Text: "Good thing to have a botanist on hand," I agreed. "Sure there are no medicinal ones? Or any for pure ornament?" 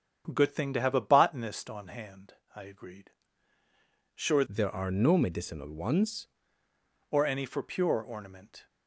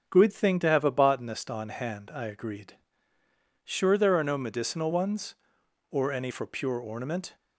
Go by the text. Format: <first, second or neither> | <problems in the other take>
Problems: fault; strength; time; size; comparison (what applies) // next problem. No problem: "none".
second | starts louder than the rest; strong; until 1.3 s; 8 dB; also in the second // changes voice from "there" to "ones"; from 4.4 to 6.2 s; 1.8 s long